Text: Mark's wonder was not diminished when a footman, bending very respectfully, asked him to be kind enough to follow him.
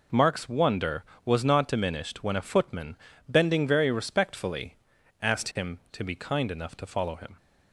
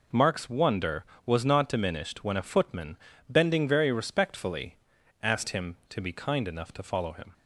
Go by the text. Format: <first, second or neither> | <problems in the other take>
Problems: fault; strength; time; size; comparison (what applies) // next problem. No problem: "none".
neither | none